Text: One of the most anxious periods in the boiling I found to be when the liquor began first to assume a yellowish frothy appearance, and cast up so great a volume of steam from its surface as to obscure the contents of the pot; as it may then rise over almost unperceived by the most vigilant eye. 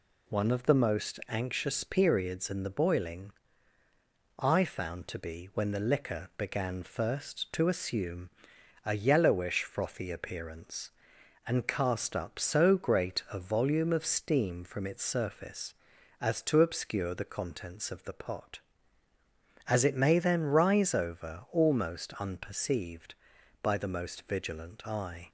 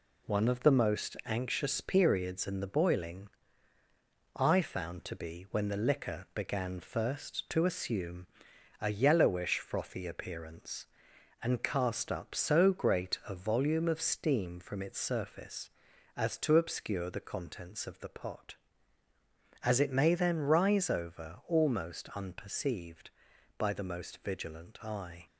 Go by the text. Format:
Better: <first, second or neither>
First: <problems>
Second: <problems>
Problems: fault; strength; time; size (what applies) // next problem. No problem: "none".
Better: first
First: pauses between "boiling" and "I"; at 3.3 s; 1.1 s long // pauses between "assume" and "a"; noticeable; at 8.3 s; 0.54 s long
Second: gets quieter; noticeable; throughout; 5 dB // pauses between "boiling" and "I"; at 3.2 s; 1.1 s long // pauses between "assume" and "a"; noticeable; at 8.2 s; 0.52 s long